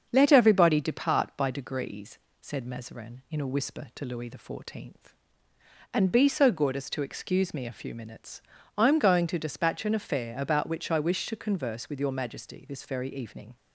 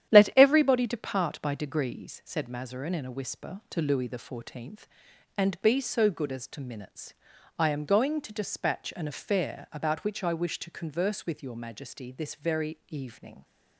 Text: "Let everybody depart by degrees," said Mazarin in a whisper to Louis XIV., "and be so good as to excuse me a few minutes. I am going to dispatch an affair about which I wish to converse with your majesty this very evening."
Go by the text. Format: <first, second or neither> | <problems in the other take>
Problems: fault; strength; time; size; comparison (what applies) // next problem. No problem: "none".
first | starts louder than the rest; strong; until 1.1 s; 10.5 dB; also in the first // skips "excuse me a few"; at 6.6 s